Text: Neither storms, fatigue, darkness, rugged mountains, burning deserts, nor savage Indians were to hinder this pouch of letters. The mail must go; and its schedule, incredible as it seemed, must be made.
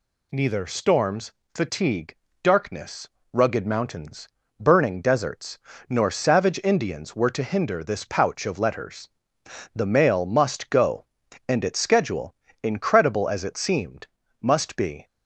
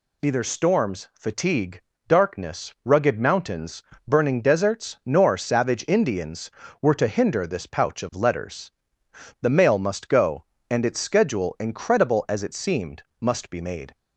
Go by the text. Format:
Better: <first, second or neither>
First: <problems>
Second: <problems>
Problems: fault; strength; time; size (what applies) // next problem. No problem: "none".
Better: second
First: stops before "made"; at 15.0 s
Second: none